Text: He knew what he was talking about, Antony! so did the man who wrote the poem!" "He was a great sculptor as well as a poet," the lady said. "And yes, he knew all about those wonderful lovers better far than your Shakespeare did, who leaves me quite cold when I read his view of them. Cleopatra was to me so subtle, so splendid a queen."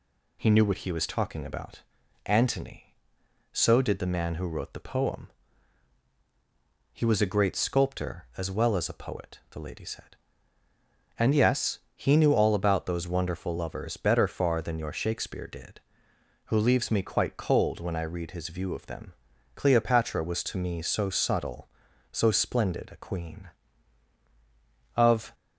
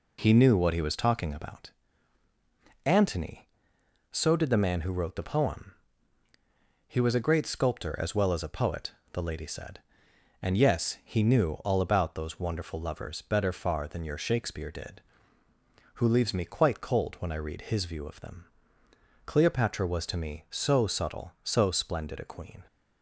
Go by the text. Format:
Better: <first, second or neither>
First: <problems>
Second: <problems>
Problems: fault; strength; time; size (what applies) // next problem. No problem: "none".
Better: second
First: goes on to say "Of"; slight; from 24.9 s on; 0.38 s long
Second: none